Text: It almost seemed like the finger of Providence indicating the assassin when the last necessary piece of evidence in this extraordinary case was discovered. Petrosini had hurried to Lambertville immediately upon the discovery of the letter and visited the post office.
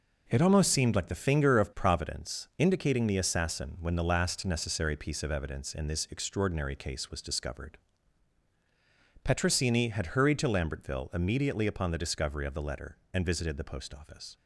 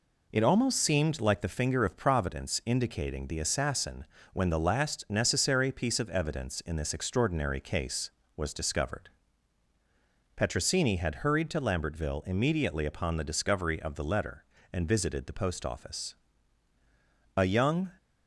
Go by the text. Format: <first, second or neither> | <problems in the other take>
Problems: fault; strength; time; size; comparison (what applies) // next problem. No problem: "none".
first | pauses between "assassin" and "when"; slight; at 4.0 s; 0.30 s long // goes on to say "A young"; from 17.3 s on; 0.56 s long